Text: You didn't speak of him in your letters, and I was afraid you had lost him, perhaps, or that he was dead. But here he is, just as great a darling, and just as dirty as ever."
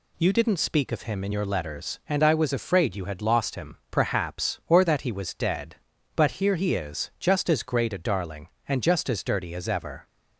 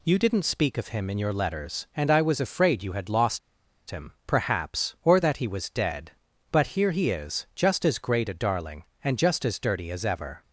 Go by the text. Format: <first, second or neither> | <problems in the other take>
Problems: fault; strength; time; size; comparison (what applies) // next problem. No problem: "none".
first | pauses between "lost" and "him"; noticeable; at 3.3 s; 0.51 s long